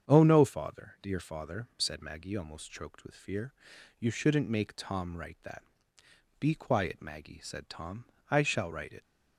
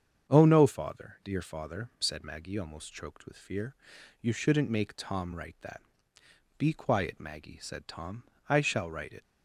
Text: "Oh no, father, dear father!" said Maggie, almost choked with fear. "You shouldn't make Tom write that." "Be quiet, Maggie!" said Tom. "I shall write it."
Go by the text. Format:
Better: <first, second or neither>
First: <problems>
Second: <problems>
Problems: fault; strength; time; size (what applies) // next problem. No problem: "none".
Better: neither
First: starts louder than the rest; strong; until 1.1 s; 7.5 dB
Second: starts louder than the rest; strong; until 1.3 s; 7.5 dB